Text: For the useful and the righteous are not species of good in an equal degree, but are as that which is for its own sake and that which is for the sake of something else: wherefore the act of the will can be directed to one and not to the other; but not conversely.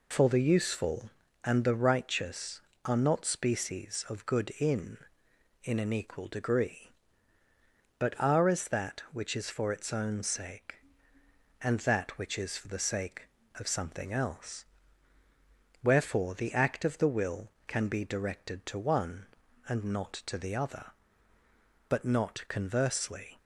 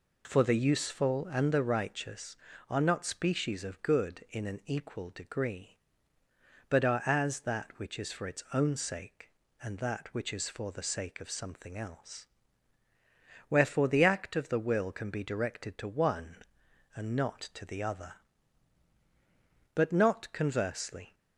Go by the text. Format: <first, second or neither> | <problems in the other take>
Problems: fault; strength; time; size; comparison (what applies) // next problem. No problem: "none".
second | says "in" twice; at 5.6 s